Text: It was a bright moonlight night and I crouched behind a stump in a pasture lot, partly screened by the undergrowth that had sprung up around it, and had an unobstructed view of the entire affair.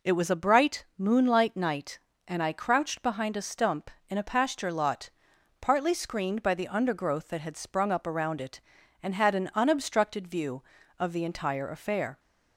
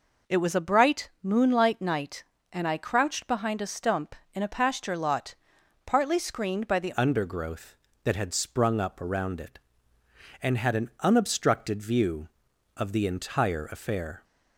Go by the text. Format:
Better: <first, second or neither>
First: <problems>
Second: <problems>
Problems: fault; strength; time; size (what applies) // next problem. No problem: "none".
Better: first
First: none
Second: changes voice at "undergrowth"; from 6.9 s on; 7.3 s long